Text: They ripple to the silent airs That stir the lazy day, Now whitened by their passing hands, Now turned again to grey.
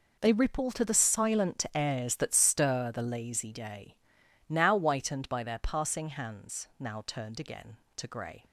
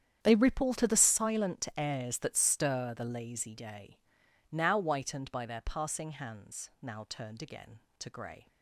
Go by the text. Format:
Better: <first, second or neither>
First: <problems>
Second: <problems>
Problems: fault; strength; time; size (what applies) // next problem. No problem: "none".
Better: first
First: none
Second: starts louder than the rest; strong; until 1.3 s; 9 dB